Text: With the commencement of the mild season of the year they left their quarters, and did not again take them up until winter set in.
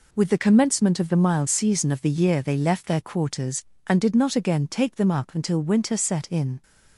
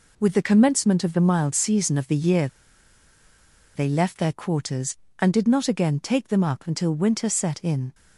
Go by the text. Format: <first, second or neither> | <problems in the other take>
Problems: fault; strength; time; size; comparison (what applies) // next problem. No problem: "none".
first | pauses between "year" and "they"; strong; at 2.4 s; 1.2 s long